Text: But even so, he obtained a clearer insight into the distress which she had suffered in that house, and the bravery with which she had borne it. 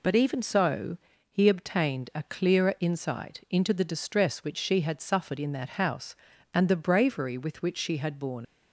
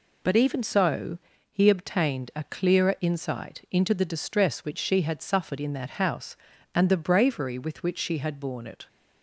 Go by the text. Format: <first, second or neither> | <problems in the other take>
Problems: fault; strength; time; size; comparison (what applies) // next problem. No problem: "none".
second | stops before "it"; at 8.4 s